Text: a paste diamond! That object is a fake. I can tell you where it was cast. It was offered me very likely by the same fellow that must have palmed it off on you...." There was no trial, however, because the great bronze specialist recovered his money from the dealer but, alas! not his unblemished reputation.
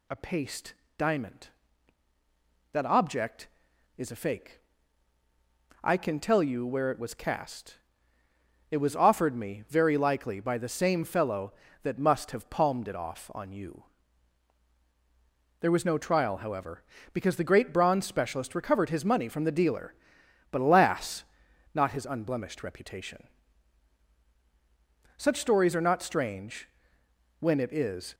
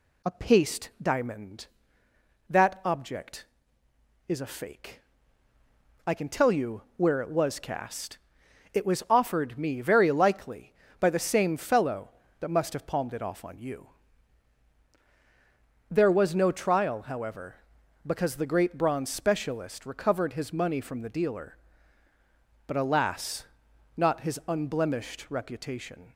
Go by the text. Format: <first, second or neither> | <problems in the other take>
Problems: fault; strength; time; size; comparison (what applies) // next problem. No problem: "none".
second | pauses between "paste" and "diamond"; slight; at 0.7 s; 0.24 s long // goes on to say "Such stories are not strange when it is"; strong; from 25.1 s on; 2.9 s long